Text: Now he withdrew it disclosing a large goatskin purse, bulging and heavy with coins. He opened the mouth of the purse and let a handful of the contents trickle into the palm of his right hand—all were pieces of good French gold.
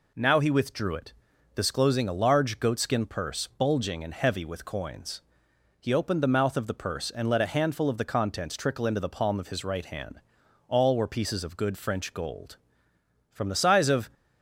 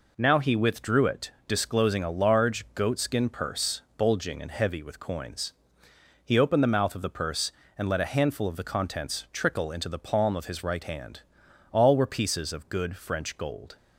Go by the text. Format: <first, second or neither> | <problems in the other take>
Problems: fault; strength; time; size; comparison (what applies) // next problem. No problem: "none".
second | pauses between "it" and "disclosing"; at 1.1 s; 0.40 s long; slight in the second // goes on to say "From the size of"; noticeable; from 13.3 s on; 0.78 s long